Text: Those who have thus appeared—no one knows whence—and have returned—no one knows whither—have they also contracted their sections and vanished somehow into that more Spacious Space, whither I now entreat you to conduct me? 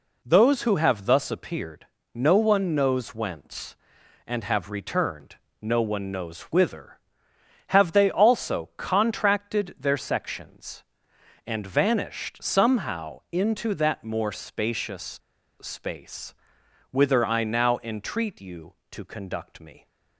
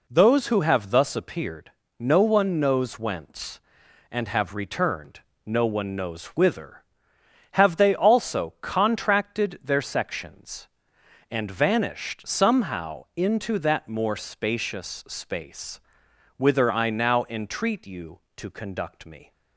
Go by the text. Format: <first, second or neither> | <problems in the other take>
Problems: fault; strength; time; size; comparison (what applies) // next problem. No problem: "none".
second | pauses between "Spacious" and "Space"; at 15.1 s; 0.44 s long